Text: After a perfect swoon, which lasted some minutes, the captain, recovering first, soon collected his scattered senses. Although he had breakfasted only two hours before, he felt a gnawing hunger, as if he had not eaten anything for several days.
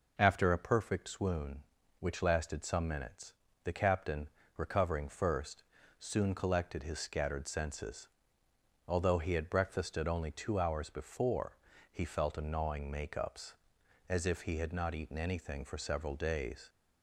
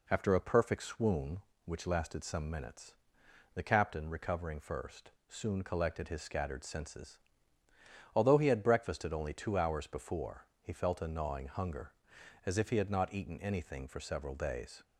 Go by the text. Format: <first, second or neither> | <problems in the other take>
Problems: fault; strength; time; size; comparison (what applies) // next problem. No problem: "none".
second | says "makeups" for "hunger"; at 12.9 s